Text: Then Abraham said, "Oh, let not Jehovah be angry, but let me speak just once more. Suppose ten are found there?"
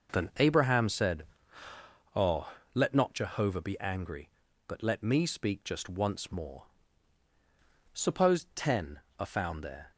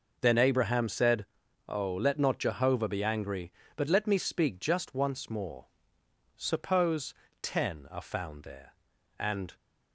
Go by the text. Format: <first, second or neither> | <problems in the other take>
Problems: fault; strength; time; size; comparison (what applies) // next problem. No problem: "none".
first | pauses between "Suppose" and "ten"; slight; at 7.1 s; 0.26 s long // goes on to say "And"; slight; from 9.1 s on; 0.38 s long